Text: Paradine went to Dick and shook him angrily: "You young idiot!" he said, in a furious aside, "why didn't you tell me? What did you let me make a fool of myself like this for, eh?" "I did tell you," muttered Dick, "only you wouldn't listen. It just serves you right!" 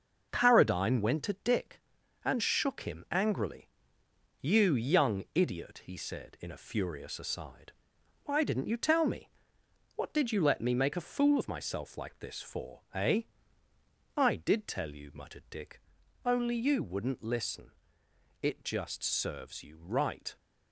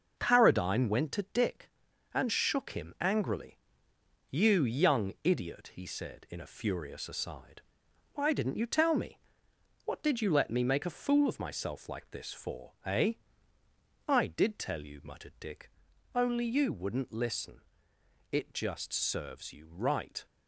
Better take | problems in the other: neither | none

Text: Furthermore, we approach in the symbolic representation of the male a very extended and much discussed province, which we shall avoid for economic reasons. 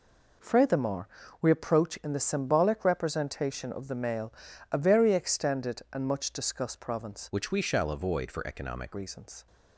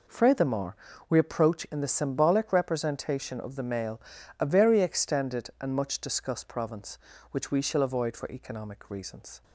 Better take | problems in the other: second | pauses between "male" and "a"; at 4.3 s; 0.40 s long; also in the second // changes voice from "which" to "economic"; from 7.3 to 8.9 s; 1.6 s long

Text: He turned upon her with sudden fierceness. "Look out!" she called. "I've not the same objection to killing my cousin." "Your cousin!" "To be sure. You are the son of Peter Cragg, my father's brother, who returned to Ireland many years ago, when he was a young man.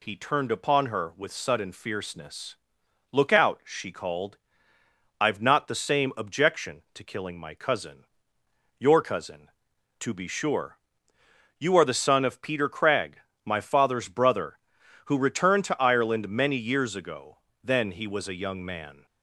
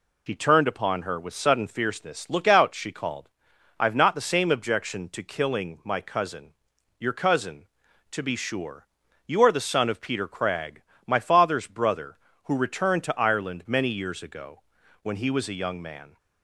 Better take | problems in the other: second | says "then" for "when"; at 17.6 s

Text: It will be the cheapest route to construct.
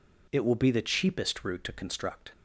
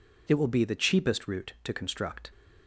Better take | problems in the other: neither | none

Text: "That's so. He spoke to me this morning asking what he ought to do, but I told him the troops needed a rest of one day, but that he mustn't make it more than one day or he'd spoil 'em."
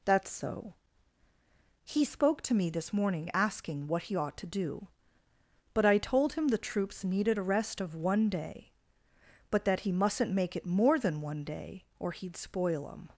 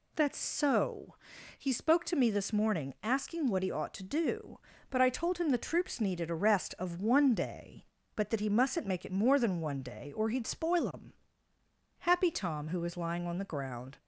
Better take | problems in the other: first | goes on to say "Happy Tom who was lying on the ground"; strong; from 12.0 s on; 1.9 s long

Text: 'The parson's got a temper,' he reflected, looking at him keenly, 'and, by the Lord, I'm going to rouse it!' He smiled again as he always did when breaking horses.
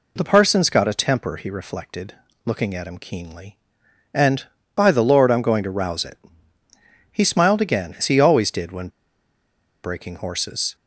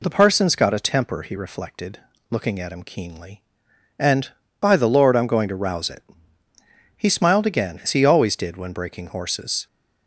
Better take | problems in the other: second | pauses between "when" and "breaking"; noticeable; at 8.8 s; 0.94 s long

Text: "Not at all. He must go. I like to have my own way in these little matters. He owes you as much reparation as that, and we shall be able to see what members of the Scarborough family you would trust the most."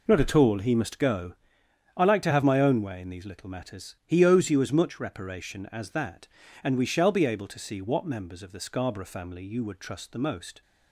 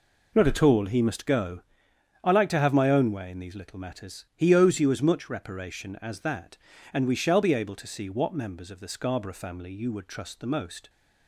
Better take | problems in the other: neither | none

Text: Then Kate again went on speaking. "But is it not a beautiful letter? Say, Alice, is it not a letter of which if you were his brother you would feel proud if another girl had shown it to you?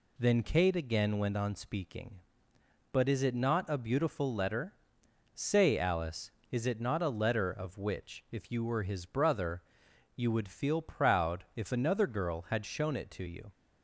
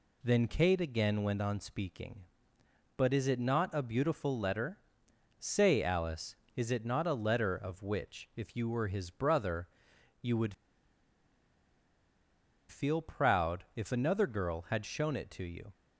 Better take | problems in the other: first | pauses between "brother" and "you"; noticeable; at 9.6 s; 0.54 s long; noticeable in the first // pauses between "would" and "feel"; strong; at 10.5 s; 2.1 s long

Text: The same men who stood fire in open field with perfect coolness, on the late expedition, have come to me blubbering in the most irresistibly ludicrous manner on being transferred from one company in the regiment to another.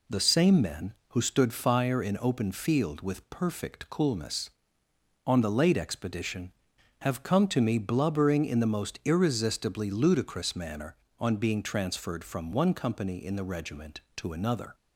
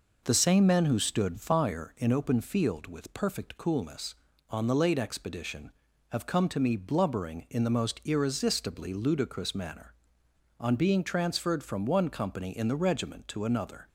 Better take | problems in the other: neither | none

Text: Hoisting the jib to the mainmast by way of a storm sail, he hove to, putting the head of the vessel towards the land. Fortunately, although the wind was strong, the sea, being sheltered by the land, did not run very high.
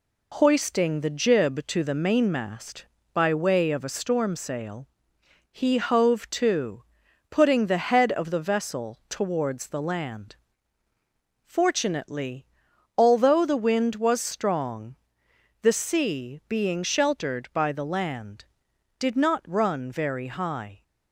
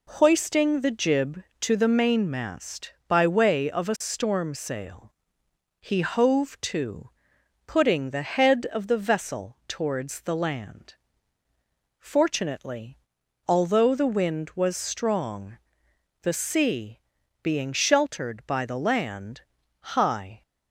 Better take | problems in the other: first | skips "did not run very"; at 19.6 s

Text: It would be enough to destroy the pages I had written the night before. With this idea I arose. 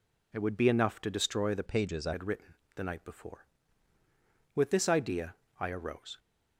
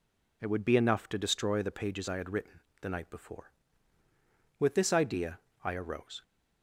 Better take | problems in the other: second | changes voice from "pages" to "I"; from 1.6 to 2.1 s; 0.5 s long // pauses between "written" and "the"; slight; at 2.5 s; 0.20 s long; slight in the second // pauses between "idea" and "I"; slight; at 5.3 s; 0.24 s long; slight in the second

